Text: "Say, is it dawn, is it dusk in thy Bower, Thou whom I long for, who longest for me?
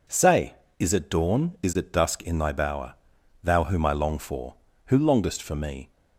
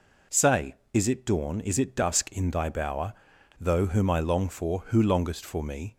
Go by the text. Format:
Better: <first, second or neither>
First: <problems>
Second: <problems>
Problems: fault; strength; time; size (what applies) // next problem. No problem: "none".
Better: first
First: none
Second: says "Though" for "Thou"; at 3.5 s